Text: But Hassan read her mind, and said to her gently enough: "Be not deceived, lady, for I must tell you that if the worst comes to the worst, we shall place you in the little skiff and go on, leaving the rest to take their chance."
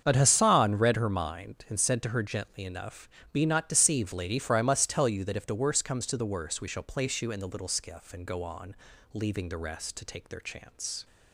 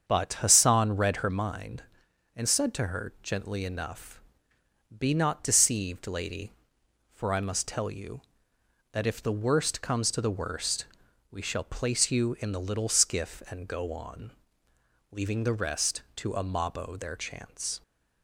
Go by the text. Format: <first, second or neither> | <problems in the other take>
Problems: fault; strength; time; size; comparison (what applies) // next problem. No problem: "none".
first | starts louder than the rest; strong; until 1.0 s; 7 dB; strong in the first // says "amabo" for "take"; at 16.3 s